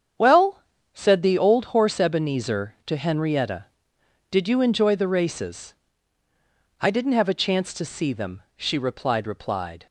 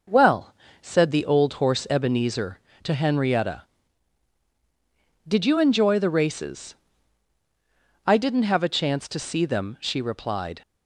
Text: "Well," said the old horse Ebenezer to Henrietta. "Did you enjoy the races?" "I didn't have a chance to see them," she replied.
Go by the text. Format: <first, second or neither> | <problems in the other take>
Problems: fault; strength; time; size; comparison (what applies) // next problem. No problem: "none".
second | starts louder than the rest; strong; until 1.5 s; 8 dB // says "replied" twice; at 9.2 s